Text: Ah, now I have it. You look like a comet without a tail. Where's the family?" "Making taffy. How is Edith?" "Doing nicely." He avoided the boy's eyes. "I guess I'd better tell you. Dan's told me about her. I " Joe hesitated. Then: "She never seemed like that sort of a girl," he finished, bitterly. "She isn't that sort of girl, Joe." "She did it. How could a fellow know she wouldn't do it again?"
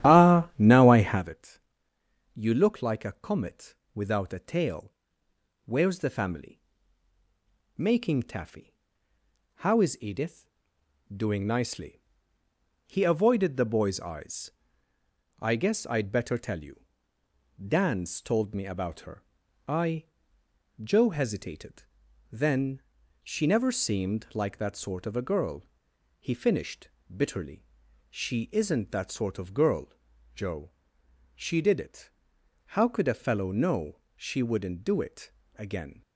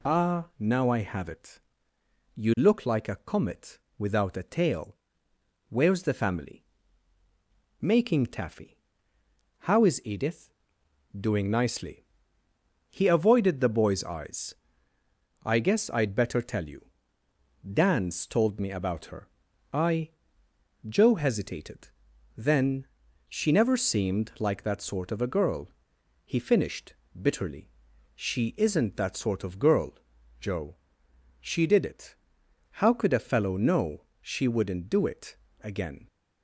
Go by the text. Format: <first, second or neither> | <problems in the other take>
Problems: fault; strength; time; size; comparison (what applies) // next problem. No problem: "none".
second | starts louder than the rest; strong; until 1.2 s; 11.5 dB // pauses between "comet" and "without"; slight; at 3.7 s; 0.18 s long; slight in the second // pauses between "know" and "she"; slight; at 33.9 s; 0.16 s long; slight in the second // pauses between "it" and "again"; slight; at 35.3 s; 0.24 s long; slight in the second